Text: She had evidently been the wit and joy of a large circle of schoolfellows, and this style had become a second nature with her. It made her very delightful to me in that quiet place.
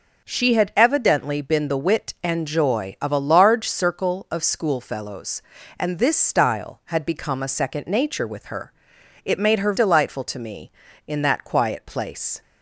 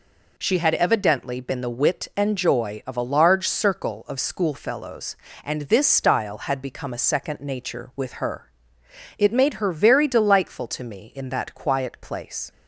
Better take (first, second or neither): second